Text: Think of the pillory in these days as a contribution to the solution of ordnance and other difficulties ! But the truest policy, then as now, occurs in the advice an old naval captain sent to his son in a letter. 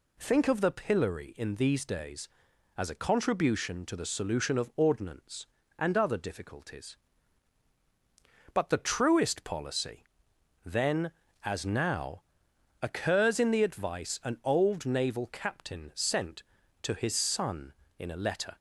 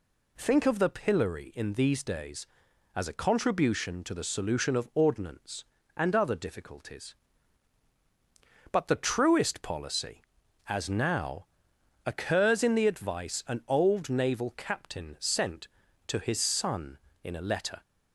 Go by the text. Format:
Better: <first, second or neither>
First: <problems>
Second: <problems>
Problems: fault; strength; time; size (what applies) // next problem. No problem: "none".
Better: first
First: none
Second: skips "then"; at 10.4 s